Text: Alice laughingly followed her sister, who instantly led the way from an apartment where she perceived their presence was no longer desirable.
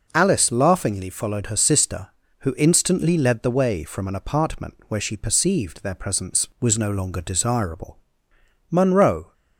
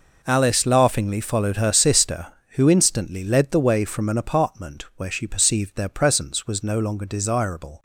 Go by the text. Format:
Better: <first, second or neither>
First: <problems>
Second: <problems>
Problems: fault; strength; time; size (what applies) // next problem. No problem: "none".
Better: second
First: goes on to say "Munro"; noticeable; from 8.7 s on; 0.62 s long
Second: none